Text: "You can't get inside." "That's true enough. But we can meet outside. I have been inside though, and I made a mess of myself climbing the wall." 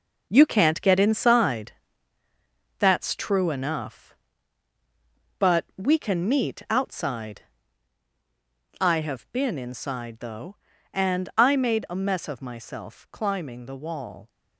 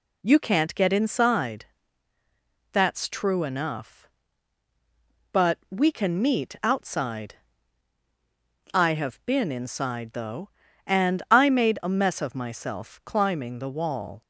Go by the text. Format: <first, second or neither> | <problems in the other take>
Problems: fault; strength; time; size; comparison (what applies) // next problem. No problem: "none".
second | gets quieter; strong; throughout; 8.5 dB